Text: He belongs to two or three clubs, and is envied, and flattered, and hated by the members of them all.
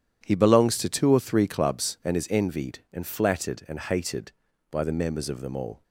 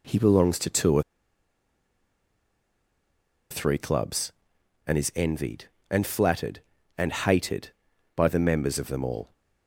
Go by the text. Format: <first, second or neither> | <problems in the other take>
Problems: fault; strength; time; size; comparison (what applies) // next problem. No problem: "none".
first | pauses between "or" and "three"; strong; at 1.0 s; 2.4 s long